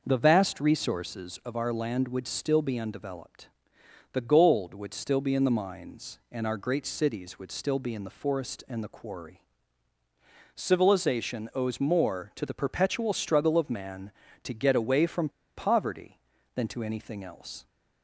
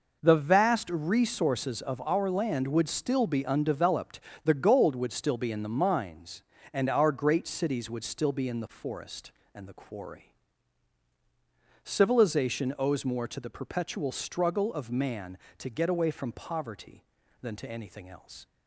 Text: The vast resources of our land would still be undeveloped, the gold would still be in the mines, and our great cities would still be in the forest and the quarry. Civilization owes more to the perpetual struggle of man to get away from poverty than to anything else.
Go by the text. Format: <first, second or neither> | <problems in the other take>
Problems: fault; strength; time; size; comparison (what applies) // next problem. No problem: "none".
second | pauses between "from" and "poverty"; slight; at 15.2 s; 0.27 s long